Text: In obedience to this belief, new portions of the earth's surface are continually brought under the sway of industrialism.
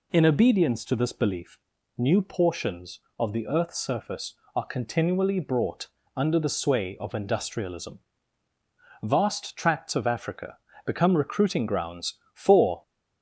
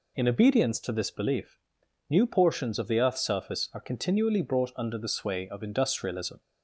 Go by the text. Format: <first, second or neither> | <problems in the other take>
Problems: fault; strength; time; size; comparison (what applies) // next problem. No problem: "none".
second | pauses between "brought" and "under"; slight; at 5.8 s; 0.30 s long // goes on to say "Vast tracts of Africa become recruiting grounds for"; strong; from 9.0 s on; 3.7 s long